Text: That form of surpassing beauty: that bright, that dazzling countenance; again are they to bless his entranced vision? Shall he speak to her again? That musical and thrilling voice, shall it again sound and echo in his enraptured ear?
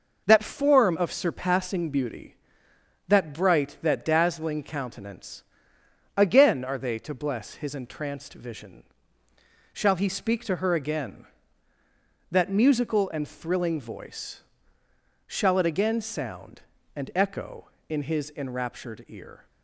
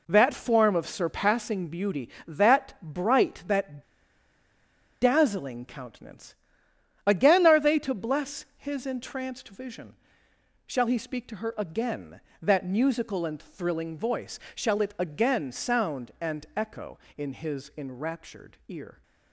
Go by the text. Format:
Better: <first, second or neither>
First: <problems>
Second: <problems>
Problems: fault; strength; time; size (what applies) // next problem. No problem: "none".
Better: first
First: none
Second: pauses between "that" and "dazzling"; at 3.8 s; 1.1 s long